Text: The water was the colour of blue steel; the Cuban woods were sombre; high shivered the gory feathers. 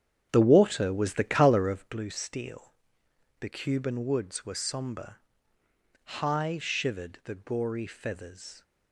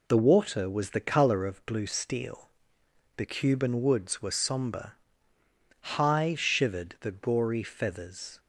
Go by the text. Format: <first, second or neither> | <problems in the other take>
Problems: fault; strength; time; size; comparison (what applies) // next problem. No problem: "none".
second | starts louder than the rest; strong; until 1.9 s; 9 dB